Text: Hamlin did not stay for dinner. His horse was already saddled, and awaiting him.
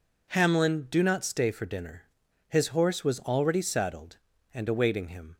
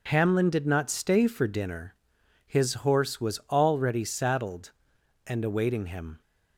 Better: second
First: says "do" for "did"; at 0.9 s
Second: none

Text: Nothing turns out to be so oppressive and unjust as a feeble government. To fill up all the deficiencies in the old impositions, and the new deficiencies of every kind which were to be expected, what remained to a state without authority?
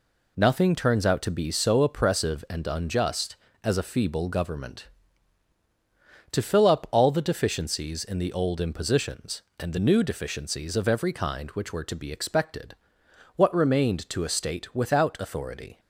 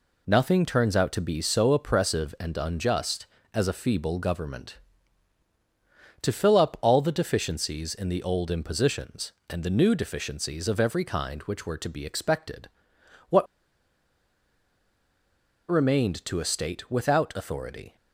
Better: first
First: none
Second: pauses between "what" and "remained"; strong; at 13.4 s; 2.2 s long

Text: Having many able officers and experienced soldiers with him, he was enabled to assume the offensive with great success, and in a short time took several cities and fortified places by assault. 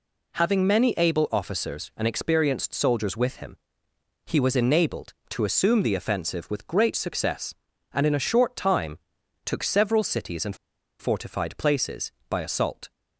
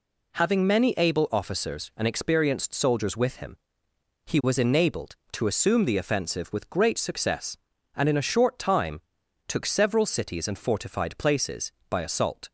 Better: second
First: pauses between "time" and "took"; noticeable; at 8.9 s; 0.46 s long // pauses between "and" and "fortified"; at 10.5 s; 0.45 s long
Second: pauses between "time" and "took"; noticeable; at 9.0 s; 0.46 s long

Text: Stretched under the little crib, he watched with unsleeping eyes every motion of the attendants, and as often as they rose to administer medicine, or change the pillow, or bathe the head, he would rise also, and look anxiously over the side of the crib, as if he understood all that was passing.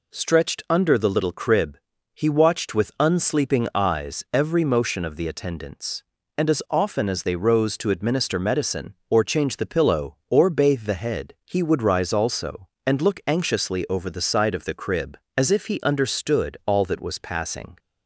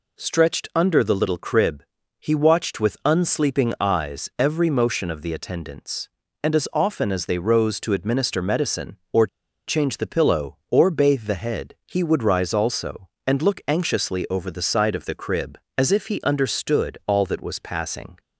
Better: first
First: none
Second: pauses between "or" and "change"; at 9.2 s; 0.40 s long

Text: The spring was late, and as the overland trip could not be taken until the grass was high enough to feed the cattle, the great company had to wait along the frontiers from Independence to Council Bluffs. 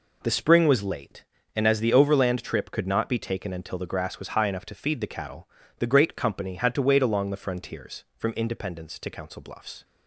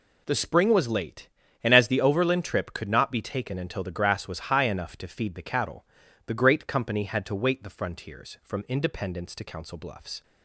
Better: first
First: none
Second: skips "along"; at 7.6 s

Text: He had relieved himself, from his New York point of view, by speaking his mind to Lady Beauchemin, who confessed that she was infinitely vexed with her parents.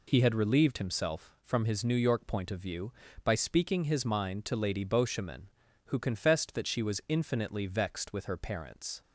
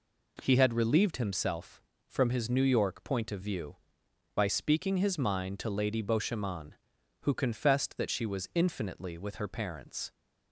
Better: first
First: none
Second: skips "vexed"; at 9.1 s

